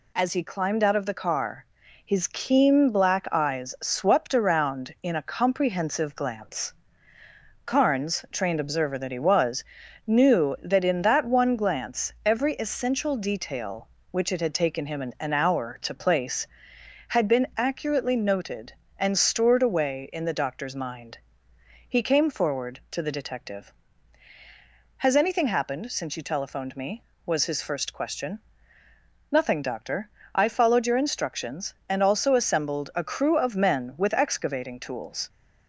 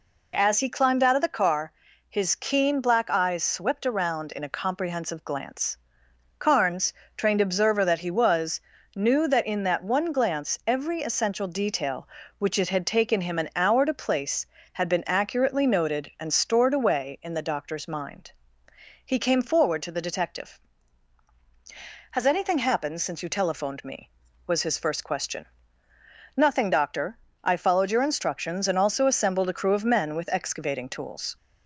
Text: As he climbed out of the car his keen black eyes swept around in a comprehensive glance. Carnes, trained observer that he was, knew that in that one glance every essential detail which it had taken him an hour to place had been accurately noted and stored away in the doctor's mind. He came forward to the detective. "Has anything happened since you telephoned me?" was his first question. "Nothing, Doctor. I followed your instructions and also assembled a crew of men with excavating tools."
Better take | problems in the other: second | pauses between "car" and "his"; at 1.6 s; 0.40 s long; also in the second // says "an" twice; at 15.2 s

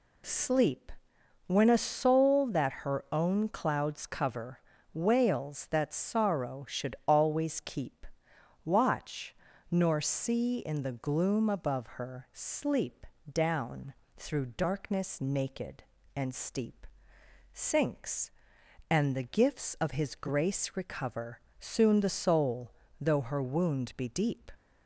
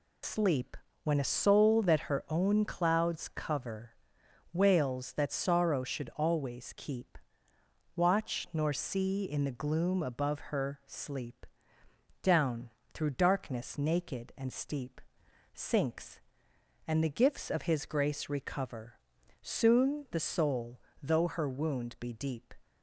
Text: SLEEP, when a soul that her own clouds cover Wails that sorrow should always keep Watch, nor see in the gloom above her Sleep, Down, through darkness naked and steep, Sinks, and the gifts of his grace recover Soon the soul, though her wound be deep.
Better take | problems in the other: first | loses the start of "SLEEP"; at 0.2 s; 75 ms // pauses between "cover" and "Wails"; noticeable; at 3.9 s; 0.60 s long; slight in the first // pauses between "keep" and "Watch"; noticeable; at 7.1 s; 0.78 s long; noticeable in the first // pauses between "recover" and "Soon"; at 18.9 s; 0.42 s long; slight in the first

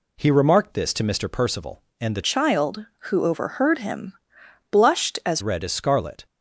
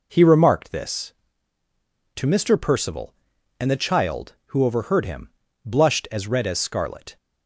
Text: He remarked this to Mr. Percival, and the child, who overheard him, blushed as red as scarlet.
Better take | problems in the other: second | changes voice from "child" to "as"; from 2.2 to 5.4 s; 3.2 s long

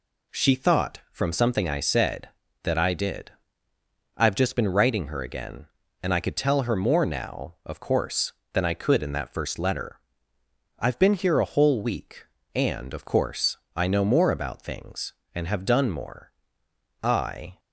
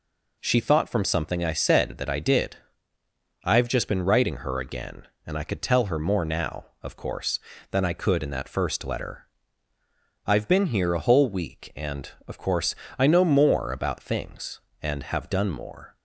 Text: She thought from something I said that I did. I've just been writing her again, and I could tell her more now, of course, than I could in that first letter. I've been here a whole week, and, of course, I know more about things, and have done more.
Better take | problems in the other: second | goes on to say "I"; from 17.0 s on; 0.56 s long

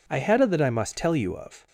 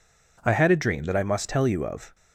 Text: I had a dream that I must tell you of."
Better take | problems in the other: second | skips "dream"; at 0.4 s

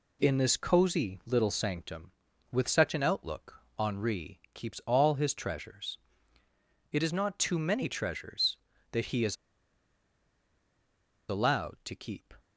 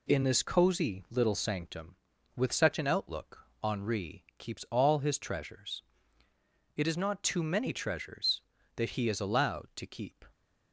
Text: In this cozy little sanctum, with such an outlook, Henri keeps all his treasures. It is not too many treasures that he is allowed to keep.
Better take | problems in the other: second | pauses between "is" and "allowed"; strong; at 9.3 s; 1.9 s long

